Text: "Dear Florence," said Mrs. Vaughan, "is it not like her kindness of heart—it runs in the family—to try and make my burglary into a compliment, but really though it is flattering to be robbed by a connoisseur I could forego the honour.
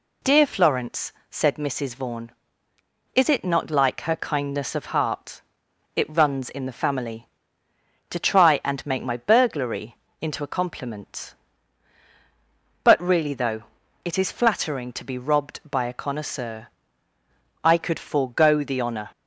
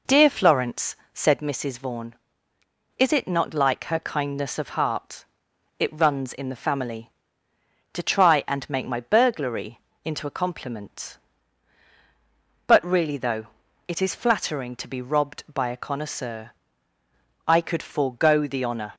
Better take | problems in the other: first | starts louder than the rest; noticeable; until 1.5 s; 4 dB // pauses between "burglary" and "into"; slight; at 9.8 s; 0.24 s long; slight in the first // pauses between "though" and "it"; at 13.4 s; 0.40 s long; also in the first // pauses between "connoisseur" and "I"; noticeable; at 16.5 s; 0.96 s long; noticeable in the first

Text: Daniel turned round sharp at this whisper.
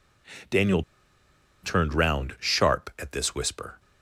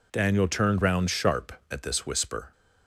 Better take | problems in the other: second | pauses between "Daniel" and "turned"; noticeable; at 0.8 s; 0.81 s long

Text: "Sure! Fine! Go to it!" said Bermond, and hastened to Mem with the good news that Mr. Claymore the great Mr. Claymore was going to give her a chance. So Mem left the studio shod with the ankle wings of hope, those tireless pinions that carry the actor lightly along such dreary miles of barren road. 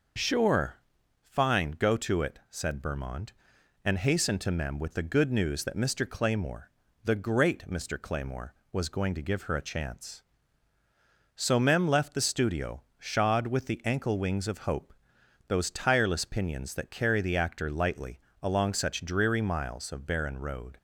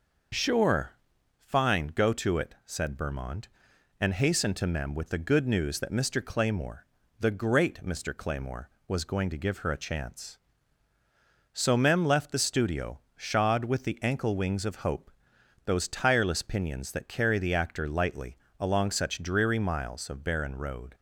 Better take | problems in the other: neither | pauses between "Claymore" and "the"; slight; the same in both // pauses between "lightly" and "along"; slight; the same in both

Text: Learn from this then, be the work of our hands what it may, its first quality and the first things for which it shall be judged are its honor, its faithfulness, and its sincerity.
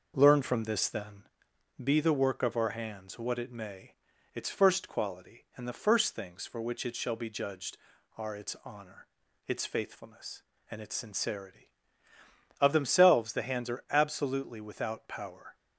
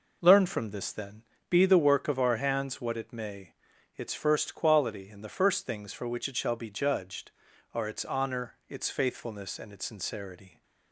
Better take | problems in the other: second | goes on to say "Of themselves the hands are absolutely without power"; strong; from 12.6 s on; 2.9 s long

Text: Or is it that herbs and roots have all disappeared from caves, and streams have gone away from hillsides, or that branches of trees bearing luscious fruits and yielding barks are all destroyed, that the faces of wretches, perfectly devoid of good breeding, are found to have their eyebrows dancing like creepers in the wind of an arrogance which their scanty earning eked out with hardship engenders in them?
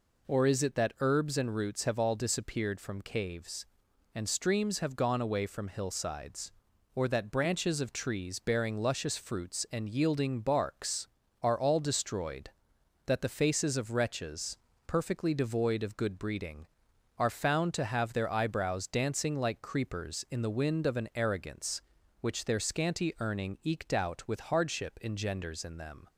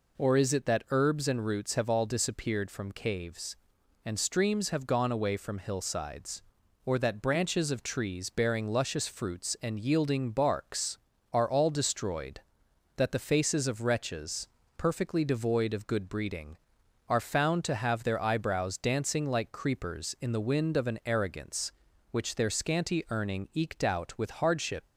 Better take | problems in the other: first | stops before "engenders in them"; at 24.8 s

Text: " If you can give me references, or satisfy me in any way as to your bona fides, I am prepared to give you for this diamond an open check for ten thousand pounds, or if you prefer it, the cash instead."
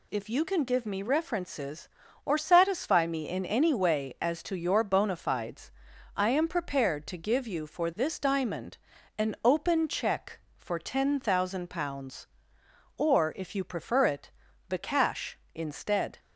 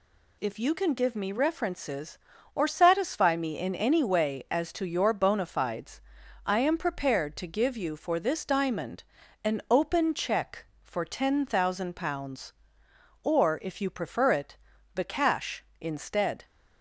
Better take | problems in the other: neither | pauses between "diamond" and "an"; the same in both

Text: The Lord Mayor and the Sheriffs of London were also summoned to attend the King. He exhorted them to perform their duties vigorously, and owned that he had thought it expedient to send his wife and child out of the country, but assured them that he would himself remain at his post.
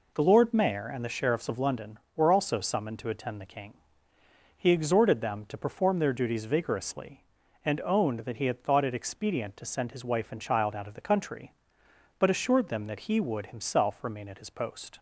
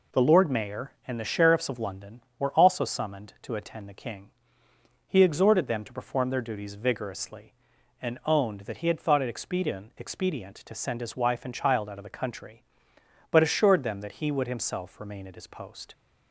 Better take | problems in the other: first | says "expedient" twice; at 9.9 s

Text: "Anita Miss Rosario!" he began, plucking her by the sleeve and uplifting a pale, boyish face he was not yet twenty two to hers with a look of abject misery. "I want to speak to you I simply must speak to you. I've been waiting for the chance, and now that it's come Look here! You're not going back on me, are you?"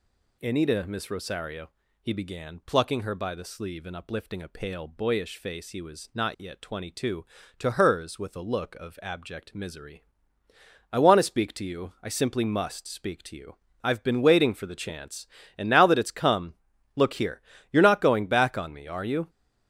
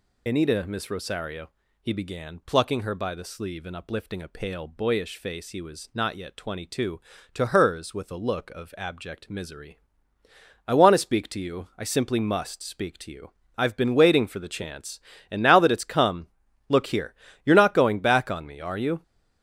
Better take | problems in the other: first | loses the start of "Anita"; at 0.2 s; 55 ms // pauses between "come" and "Look"; at 16.2 s; 0.40 s long; also in the first

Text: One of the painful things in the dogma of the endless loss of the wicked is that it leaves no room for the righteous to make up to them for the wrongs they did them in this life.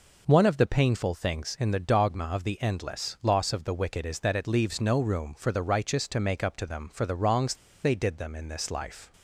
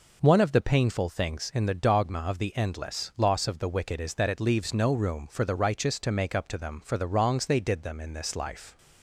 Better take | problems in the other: second | pauses between "wrongs" and "they"; slight; at 7.5 s; 0.29 s long

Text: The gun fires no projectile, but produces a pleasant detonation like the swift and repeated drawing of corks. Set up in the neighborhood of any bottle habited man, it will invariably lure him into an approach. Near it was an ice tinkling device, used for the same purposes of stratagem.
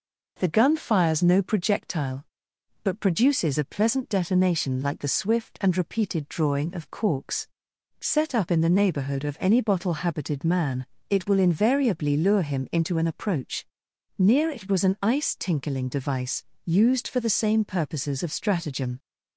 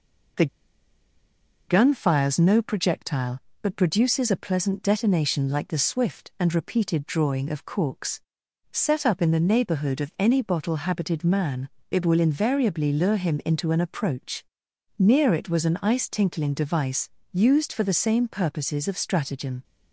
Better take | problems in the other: first | pauses between "The" and "gun"; at 0.4 s; 1.2 s long

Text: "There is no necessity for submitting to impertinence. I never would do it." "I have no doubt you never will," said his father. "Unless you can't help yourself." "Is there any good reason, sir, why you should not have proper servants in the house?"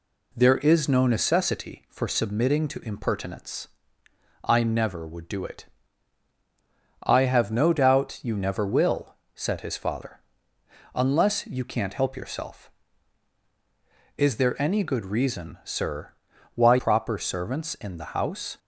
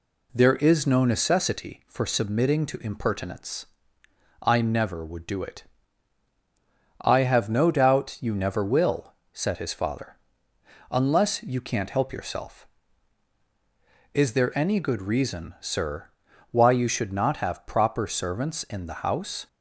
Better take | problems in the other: second | skips "you should not have"; at 16.7 s

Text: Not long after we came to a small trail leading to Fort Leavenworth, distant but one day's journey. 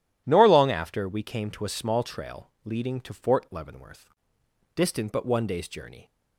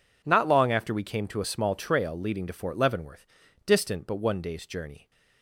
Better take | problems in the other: second | says "Nor" for "Not"; at 0.2 s

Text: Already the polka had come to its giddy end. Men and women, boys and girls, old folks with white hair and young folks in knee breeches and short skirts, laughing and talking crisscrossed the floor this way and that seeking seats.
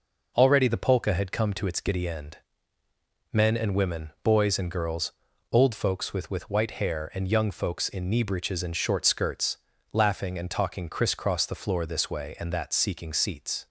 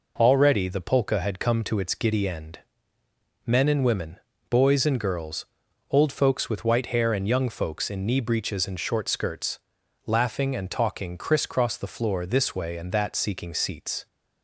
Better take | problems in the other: second | says "with" twice; at 6.3 s

